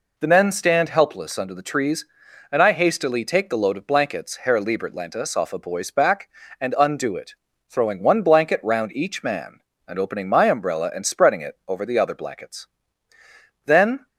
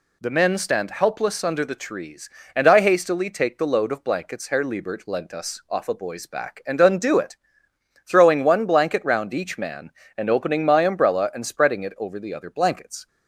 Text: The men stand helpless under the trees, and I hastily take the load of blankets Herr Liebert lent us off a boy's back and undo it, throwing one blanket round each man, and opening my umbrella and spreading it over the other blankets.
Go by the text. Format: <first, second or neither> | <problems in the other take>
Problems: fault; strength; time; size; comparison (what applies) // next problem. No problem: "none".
second | goes on to say "Then"; slight; from 13.6 s on; 0.42 s long